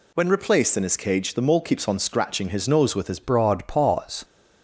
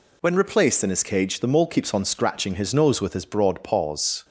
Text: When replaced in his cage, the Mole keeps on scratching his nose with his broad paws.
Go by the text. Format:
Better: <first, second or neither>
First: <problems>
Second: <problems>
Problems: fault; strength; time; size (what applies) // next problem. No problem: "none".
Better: second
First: changes voice at "broad"; from 3.2 s on; 1.0 s long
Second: none